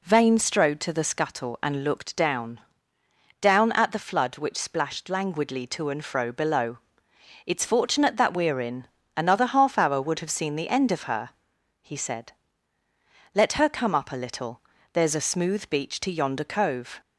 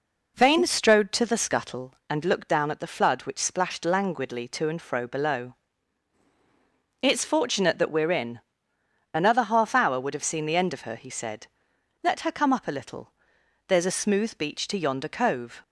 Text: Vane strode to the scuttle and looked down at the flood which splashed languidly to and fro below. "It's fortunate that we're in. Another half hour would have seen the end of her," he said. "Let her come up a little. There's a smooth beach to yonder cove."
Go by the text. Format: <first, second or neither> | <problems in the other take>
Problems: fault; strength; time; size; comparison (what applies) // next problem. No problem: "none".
second | says "down" twice; at 3.4 s